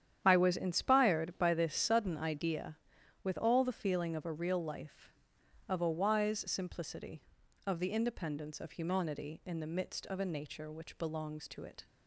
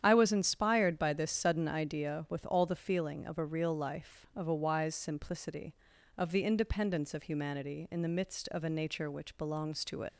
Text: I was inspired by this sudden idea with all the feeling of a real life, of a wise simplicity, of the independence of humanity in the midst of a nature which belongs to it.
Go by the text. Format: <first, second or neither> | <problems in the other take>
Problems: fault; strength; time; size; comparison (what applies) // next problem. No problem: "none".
first | starts louder than the rest; strong; until 1.0 s; 9.5 dB; strong in the first // leaves "it" unfinished; at 10.0 s; 35 ms